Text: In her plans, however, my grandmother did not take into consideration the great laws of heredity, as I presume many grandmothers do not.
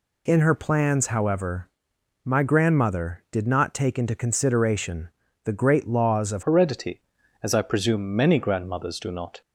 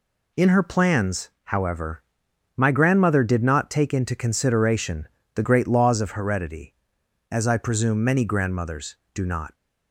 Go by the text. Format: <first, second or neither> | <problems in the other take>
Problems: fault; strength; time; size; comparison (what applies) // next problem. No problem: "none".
second | pauses between "consideration" and "the"; slight; at 5.1 s; 0.34 s long; slight in the second // changes voice at "heredity"; from 6.4 s on; 3.0 s long